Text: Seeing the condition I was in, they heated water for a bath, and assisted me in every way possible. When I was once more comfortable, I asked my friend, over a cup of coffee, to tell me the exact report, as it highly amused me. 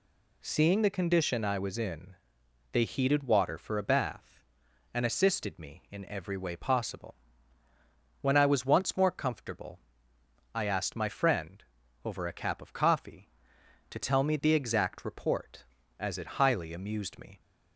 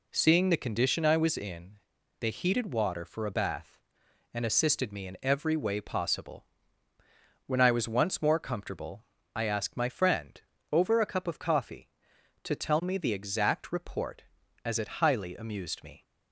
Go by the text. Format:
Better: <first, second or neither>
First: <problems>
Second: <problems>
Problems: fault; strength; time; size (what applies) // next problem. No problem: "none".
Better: second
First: says "cap" for "cup"; at 12.3 s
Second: none